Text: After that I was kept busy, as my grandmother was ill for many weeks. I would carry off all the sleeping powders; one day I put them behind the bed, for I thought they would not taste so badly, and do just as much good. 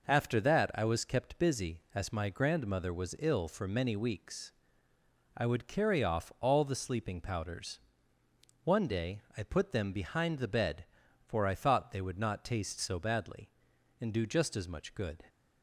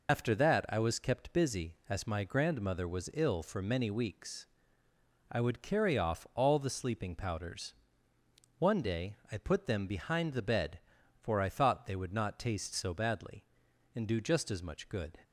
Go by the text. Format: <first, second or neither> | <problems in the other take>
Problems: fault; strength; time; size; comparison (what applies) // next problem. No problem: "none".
first | loses the start of "After"; at 0.0 s; 105 ms